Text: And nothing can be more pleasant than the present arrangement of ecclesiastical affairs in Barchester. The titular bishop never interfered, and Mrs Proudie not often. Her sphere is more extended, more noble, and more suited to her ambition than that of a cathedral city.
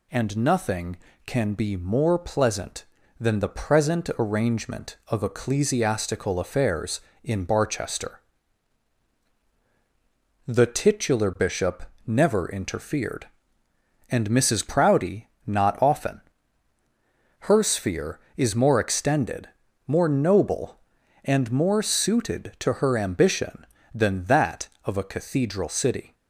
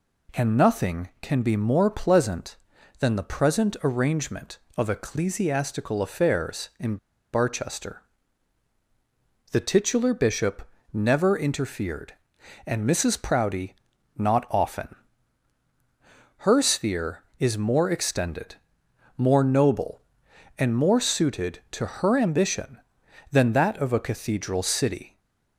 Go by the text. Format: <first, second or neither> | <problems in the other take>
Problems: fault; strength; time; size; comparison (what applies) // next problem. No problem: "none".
first | pauses between "in" and "Barchester"; at 6.9 s; 0.37 s long // pauses between "bishop" and "never"; slight; at 10.6 s; 0.24 s long; slight in the first // pauses between "Proudie" and "not"; at 13.7 s; 0.42 s long; slight in the first // stays silent after the last word; slight; from 25.0 s on; 0.5 s long